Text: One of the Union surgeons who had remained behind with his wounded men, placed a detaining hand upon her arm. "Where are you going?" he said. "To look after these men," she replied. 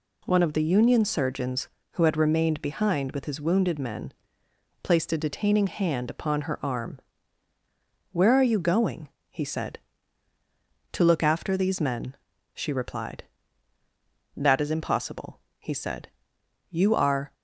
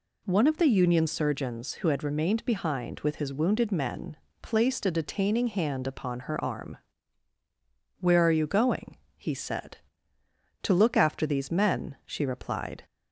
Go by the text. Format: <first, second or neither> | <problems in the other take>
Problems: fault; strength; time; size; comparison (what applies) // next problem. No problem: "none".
second | goes on to say "That is impossible he said You are"; strong; from 14.3 s on; 2.9 s long